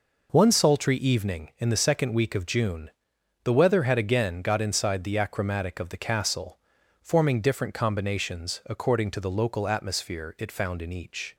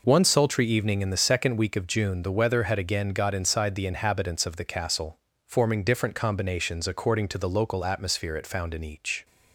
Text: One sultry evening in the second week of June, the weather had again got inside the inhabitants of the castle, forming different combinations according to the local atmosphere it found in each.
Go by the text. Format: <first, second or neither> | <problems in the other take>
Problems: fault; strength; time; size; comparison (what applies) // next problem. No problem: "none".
second | says "achromatic" for "inhabitants"; at 5.1 s